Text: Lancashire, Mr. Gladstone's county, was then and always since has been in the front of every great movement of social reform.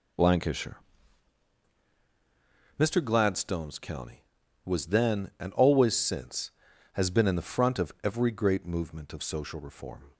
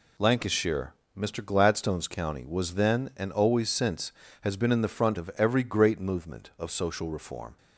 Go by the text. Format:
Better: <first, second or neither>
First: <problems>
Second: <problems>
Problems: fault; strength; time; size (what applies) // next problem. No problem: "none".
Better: neither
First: none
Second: none